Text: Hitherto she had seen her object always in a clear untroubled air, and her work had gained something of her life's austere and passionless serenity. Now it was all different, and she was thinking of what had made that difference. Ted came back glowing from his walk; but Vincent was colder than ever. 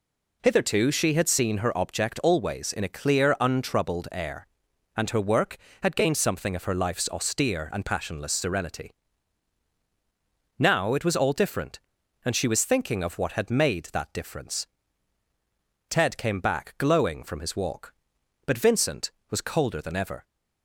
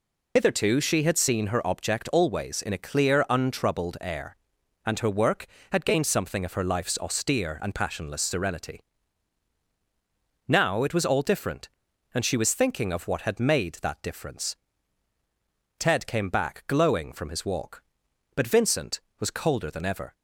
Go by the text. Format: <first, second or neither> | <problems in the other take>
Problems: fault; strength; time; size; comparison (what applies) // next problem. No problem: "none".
first | loses the start of "Hitherto"; at 0.3 s; 40 ms